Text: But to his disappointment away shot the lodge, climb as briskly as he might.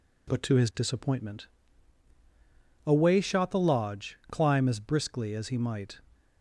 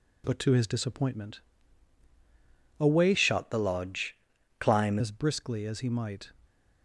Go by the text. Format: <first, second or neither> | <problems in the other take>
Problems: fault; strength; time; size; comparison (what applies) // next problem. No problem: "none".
first | pauses between "disappointment" and "away"; strong; at 1.4 s; 1.3 s long; strong in the first // changes voice from "shot" to "climb"; from 3.1 to 4.9 s; 1.8 s long